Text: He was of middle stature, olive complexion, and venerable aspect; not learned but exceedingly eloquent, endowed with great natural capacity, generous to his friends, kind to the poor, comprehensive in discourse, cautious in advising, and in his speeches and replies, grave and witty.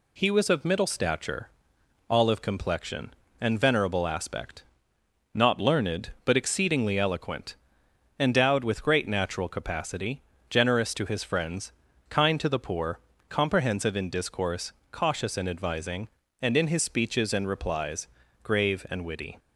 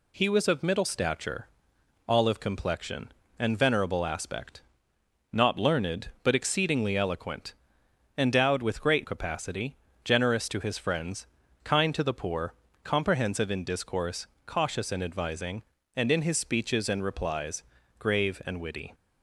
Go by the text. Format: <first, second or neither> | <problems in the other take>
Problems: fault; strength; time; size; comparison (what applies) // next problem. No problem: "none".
first | skips "natural"; at 9.0 s